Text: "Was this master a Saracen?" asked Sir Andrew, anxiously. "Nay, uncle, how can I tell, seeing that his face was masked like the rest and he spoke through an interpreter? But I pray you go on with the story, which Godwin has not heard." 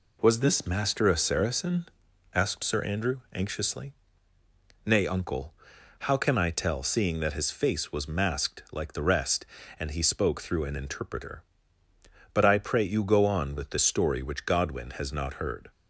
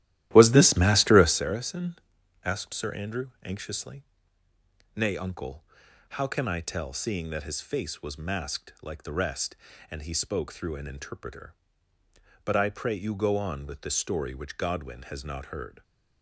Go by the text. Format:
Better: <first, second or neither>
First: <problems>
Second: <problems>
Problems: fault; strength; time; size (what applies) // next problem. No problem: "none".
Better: first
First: none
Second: starts louder than the rest; strong; until 1.5 s; 14 dB